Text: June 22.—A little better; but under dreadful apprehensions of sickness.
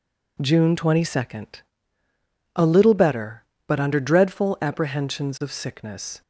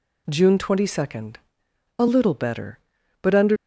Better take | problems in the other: first | stops before "dreadful apprehensions of sickness"; at 3.5 s

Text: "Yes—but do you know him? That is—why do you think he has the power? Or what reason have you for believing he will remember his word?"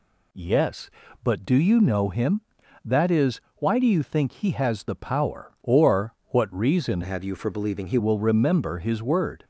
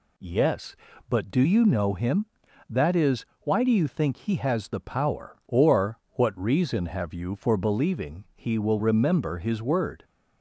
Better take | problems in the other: second | changes voice from "have" to "he"; from 7.0 to 7.9 s; 0.9 s long

